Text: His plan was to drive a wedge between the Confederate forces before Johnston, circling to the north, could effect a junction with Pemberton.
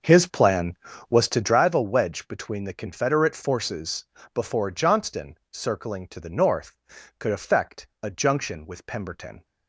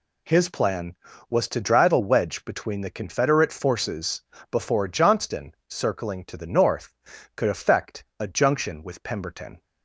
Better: second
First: starts louder than the rest; until 1.6 s; 6 dB // pauses between "forces" and "before"; slight; at 4.0 s; 0.28 s long // pauses between "effect" and "a"; slight; at 7.8 s; 0.16 s long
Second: pauses between "forces" and "before"; slight; at 4.2 s; 0.28 s long // pauses between "effect" and "a"; slight; at 8.0 s; 0.16 s long

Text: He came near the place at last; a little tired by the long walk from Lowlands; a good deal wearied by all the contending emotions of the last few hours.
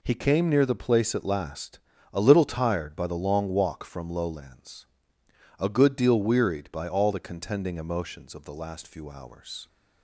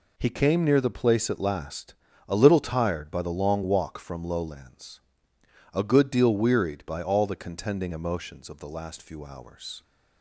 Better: neither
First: none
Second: none

